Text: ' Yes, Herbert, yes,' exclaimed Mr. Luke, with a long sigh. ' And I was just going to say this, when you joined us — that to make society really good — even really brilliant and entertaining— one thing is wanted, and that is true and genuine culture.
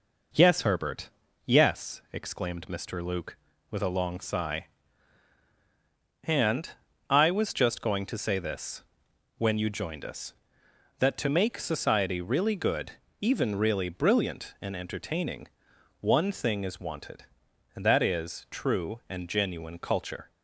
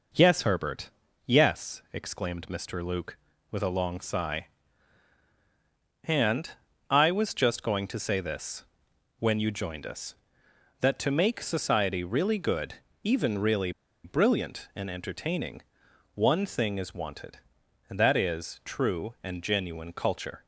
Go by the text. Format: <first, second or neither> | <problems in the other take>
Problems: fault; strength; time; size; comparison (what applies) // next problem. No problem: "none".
first | pauses between "And" and "I"; at 6.5 s; 0.40 s long; also in the first // pauses between "really" and "brilliant"; slight; at 13.7 s; 0.33 s long